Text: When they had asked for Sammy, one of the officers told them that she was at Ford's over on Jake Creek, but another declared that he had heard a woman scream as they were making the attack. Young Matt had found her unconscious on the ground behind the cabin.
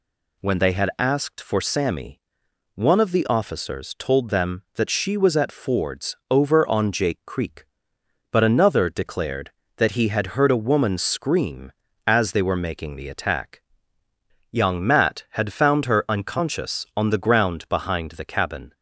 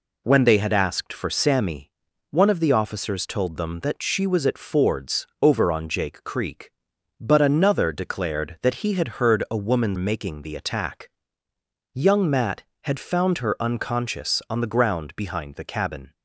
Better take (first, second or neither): first